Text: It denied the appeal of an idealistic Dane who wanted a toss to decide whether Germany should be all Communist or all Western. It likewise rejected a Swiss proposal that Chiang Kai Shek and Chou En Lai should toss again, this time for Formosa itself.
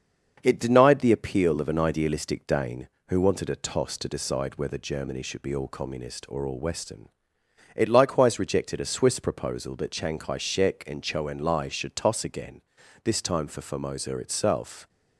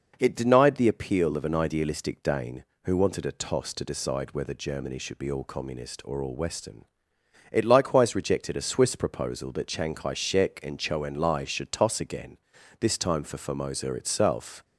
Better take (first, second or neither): second